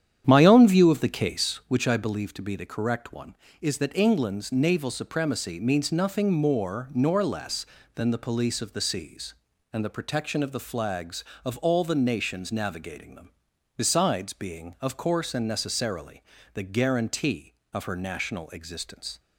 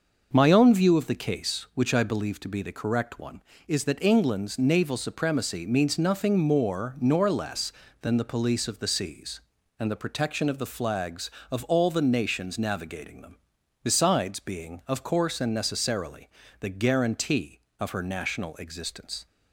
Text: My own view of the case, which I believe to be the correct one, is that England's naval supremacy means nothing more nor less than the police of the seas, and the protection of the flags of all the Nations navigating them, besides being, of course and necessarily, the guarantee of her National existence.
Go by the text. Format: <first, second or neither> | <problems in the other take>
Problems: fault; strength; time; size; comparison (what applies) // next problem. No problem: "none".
second | starts louder than the rest; strong; until 1.8 s; 9.5 dB